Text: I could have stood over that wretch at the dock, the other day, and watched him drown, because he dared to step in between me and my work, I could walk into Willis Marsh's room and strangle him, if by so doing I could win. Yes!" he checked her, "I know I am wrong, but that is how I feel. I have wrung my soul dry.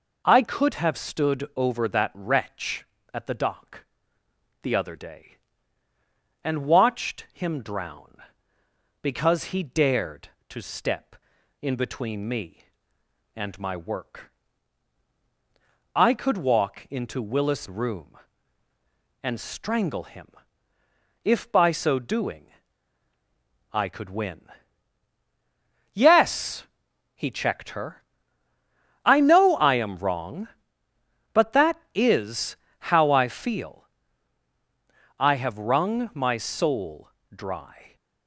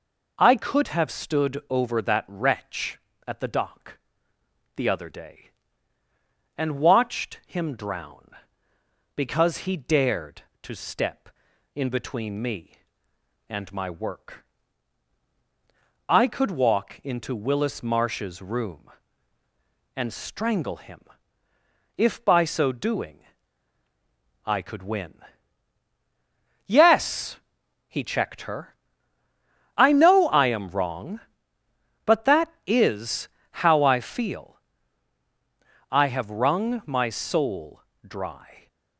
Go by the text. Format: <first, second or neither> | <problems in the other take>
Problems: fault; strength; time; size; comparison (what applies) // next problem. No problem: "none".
second | skips "Marsh's"; at 17.6 s // pauses between "doing" and "I"; strong; at 22.4 s; 1.2 s long; strong in the second // pauses between "is" and "how"; at 32.5 s; 0.38 s long; also in the second // pauses between "soul" and "dry"; slight; at 37.1 s; 0.22 s long; slight in the second